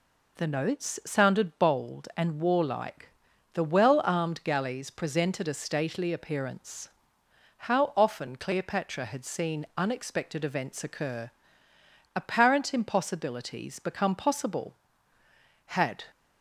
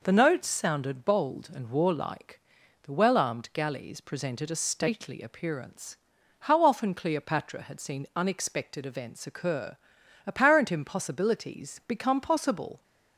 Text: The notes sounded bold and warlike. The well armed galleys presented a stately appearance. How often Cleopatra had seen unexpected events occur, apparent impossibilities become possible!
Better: second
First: goes on to say "Had"; slight; from 15.6 s on; 0.38 s long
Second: none

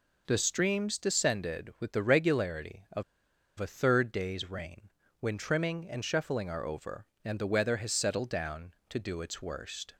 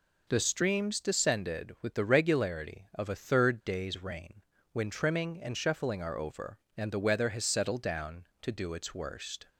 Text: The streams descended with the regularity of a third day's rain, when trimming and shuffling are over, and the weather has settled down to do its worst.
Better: second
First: pauses between "of" and "a"; noticeable; at 3.0 s; 0.56 s long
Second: none

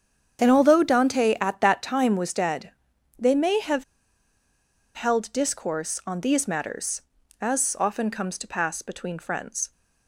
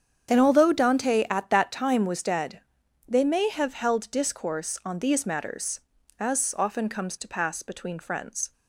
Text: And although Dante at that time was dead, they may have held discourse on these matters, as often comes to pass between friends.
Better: second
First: starts louder than the rest; strong; until 1.4 s; 8 dB // pauses between "have" and "held"; at 3.8 s; 1.1 s long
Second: starts louder than the rest; strong; until 1.3 s; 8 dB

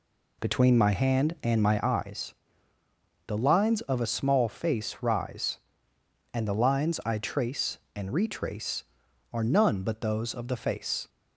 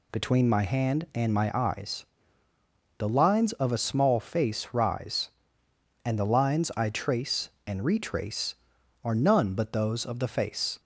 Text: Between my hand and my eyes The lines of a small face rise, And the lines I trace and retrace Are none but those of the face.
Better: second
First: starts louder than the rest; slight; until 2.0 s; 2 dB // pauses between "eyes" and "The"; noticeable; at 2.3 s; 0.94 s long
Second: pauses between "eyes" and "The"; noticeable; at 2.0 s; 0.94 s long

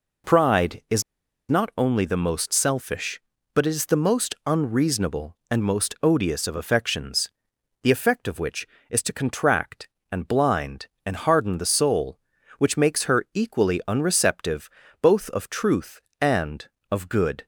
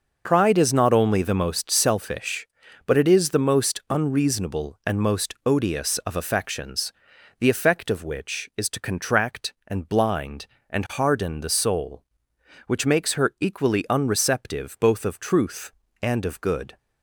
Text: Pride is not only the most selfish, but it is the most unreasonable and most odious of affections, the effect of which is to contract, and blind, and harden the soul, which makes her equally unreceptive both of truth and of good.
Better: second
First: pauses between "is" and "not"; noticeable; at 1.0 s; 0.48 s long // pauses between "unreceptive" and "both"; slight; at 14.6 s; 0.32 s long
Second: none

